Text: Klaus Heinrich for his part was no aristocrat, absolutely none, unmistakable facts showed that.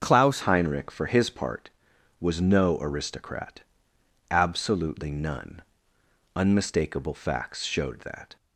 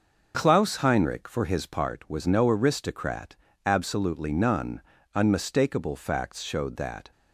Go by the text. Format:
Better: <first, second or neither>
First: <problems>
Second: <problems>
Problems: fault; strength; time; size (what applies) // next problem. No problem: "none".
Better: second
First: starts louder than the rest; until 1.0 s; 6.5 dB // changes voice at "Heinrich"; from 0.4 s on; 7.9 s long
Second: none